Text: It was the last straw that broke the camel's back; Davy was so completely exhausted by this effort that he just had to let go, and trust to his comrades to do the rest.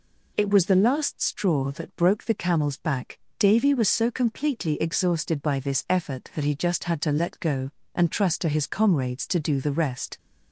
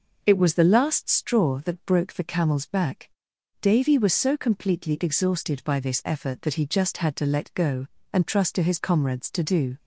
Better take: first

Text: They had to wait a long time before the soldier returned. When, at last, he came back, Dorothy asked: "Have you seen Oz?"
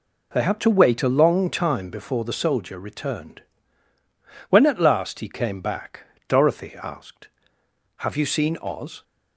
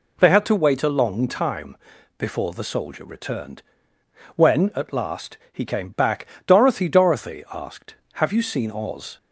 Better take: first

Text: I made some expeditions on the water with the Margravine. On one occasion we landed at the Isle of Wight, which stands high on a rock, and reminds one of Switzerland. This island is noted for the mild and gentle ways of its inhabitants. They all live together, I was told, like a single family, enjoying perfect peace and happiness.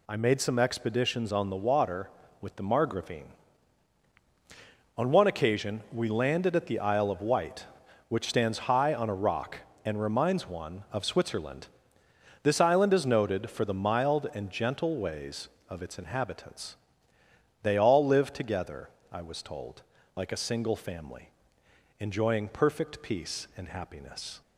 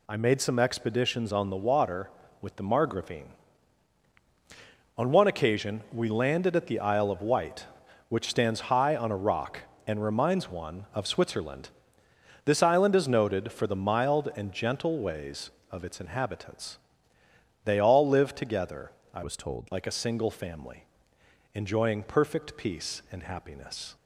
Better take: first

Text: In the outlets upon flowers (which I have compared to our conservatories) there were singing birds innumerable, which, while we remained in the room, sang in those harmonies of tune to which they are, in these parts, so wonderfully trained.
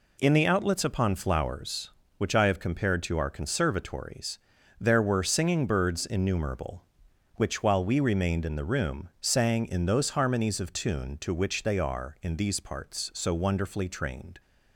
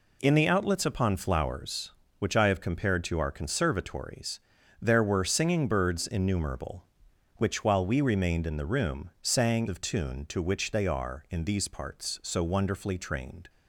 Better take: first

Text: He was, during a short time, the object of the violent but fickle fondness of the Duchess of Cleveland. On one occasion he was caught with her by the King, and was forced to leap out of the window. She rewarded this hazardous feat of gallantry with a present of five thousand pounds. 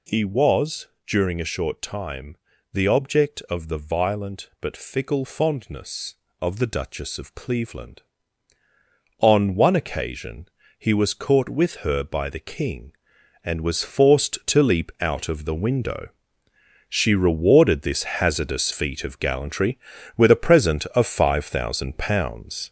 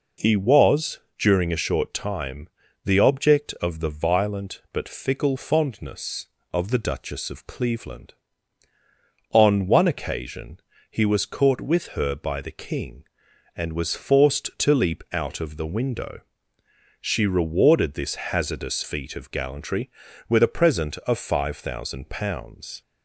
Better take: second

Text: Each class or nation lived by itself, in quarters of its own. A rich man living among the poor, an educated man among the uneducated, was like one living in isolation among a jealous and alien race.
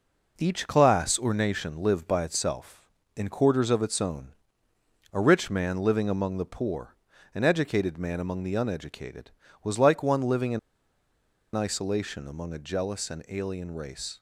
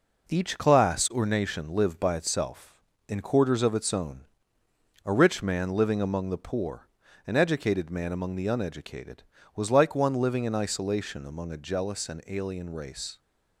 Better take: second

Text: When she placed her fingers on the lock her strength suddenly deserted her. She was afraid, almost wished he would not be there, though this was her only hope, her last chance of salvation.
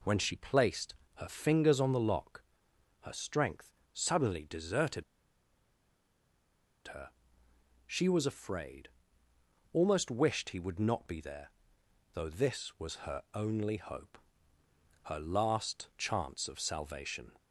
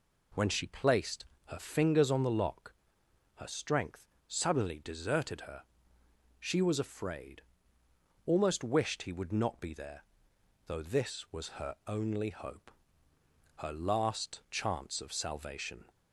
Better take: second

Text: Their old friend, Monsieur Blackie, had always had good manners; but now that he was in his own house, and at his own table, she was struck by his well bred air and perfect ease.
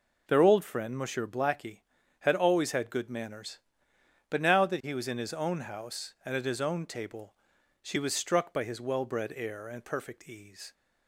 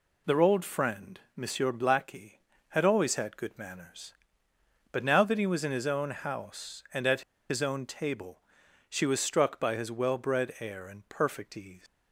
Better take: first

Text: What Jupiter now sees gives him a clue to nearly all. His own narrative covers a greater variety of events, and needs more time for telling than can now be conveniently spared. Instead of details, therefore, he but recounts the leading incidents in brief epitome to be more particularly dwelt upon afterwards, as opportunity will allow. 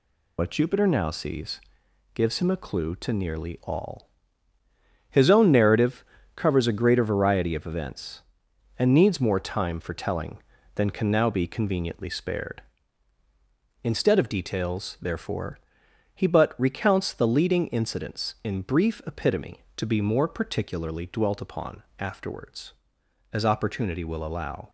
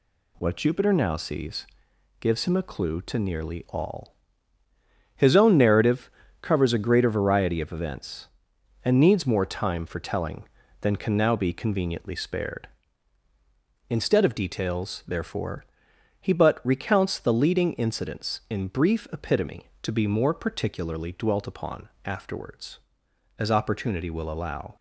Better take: second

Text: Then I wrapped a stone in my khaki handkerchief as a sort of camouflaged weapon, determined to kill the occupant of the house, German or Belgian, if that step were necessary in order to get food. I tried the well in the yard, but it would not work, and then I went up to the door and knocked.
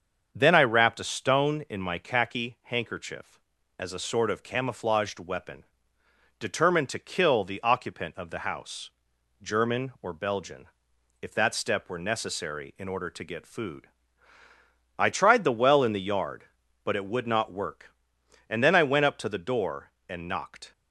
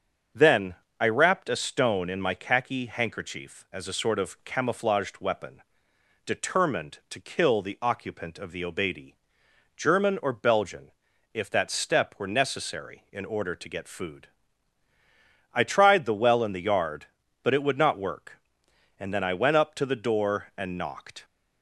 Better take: first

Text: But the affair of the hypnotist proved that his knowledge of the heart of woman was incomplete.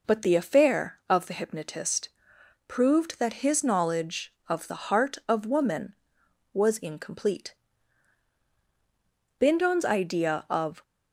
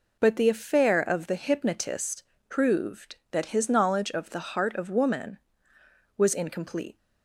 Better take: second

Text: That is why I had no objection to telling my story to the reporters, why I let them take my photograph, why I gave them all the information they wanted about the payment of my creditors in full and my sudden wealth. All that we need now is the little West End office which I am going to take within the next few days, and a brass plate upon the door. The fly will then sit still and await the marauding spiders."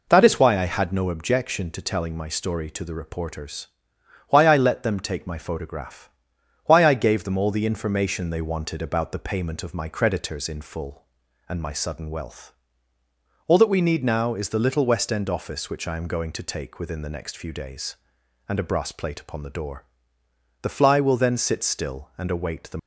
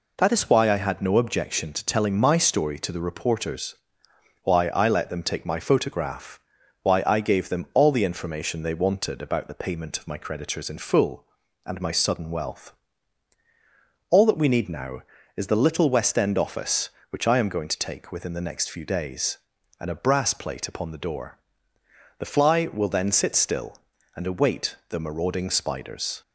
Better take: second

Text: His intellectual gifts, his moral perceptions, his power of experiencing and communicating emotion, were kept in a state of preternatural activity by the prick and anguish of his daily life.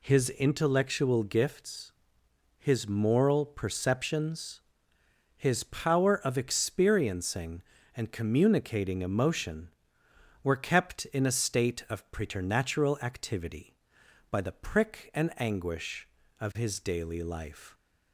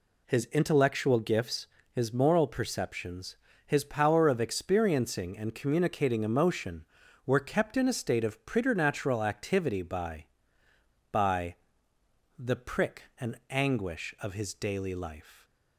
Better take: first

